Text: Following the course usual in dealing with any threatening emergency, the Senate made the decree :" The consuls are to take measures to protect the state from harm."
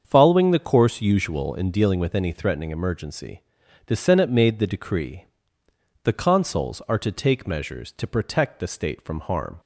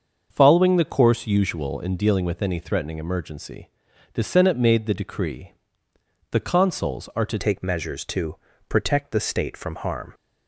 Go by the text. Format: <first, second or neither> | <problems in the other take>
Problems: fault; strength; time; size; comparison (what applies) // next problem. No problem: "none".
first | starts louder than the rest; until 1.3 s; 6.5 dB; strong in the first // changes voice at "take"; from 7.3 s on; 2.8 s long // pauses between "to" and "protect"; slight; at 8.3 s; 0.32 s long